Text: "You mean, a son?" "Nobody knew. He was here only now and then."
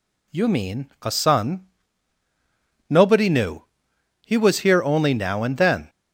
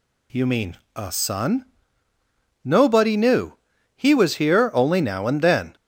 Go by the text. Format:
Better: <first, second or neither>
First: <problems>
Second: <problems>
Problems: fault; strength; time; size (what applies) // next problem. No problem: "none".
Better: neither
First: none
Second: none